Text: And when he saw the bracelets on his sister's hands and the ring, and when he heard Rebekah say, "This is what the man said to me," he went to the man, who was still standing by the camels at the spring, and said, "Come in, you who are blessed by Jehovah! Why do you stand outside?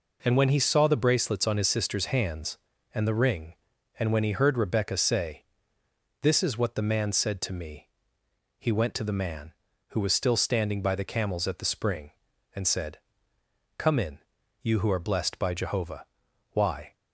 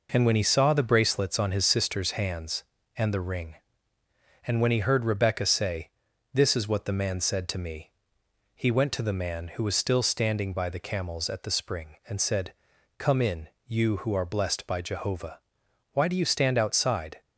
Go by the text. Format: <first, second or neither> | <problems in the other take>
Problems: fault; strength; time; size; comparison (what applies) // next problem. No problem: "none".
second | stops before "do you stand outside"; at 16.9 s